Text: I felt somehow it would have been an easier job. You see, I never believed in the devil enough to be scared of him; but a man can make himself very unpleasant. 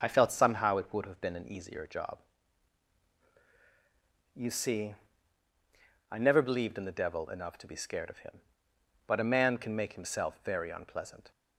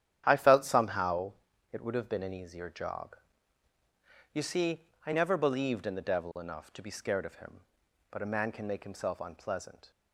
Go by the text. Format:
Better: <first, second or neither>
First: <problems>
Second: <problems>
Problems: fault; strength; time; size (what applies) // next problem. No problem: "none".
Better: first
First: starts louder than the rest; strong; until 1.0 s; 7 dB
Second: starts louder than the rest; strong; until 1.2 s; 10 dB // pauses between "somehow" and "it"; at 1.3 s; 0.38 s long // skips "very"; at 9.2 s